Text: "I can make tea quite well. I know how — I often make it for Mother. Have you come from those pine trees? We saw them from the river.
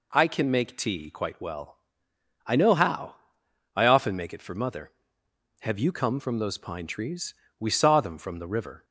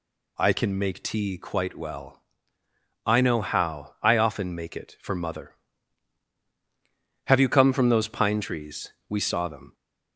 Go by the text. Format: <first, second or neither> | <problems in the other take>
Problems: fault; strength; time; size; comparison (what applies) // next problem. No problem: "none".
first | stops before "from the river"; at 9.7 s